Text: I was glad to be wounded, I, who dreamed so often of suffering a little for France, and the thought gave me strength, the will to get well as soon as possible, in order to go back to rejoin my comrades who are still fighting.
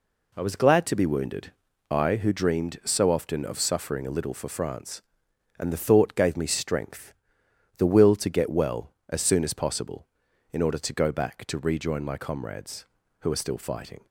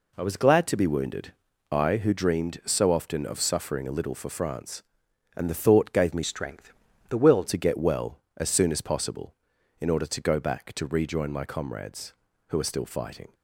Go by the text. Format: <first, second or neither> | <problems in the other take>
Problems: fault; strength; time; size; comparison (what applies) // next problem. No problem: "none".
first | changes voice from "strength" to "will"; from 6.2 to 7.4 s; 1.2 s long